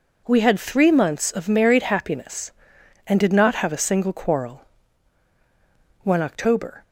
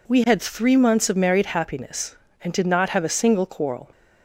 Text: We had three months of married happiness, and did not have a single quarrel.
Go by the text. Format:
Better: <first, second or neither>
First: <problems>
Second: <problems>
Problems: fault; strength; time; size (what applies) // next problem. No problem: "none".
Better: second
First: goes on to say "One October"; noticeable; from 6.0 s on; 0.80 s long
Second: none